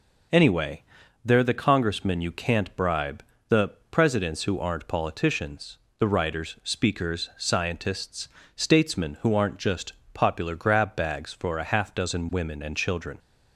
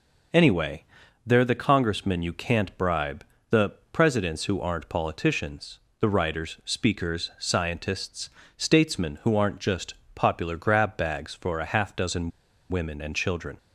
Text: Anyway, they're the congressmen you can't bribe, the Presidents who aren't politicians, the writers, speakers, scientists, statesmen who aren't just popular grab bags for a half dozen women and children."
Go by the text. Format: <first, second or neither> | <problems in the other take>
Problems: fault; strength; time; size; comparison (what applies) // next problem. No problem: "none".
first | pauses between "the" and "Presidents"; slight; at 3.7 s; 0.18 s long; slight in the first // pauses between "just" and "popular"; slight; at 9.9 s; 0.20 s long; slight in the first // pauses between "dozen" and "women"; at 12.2 s; 0.40 s long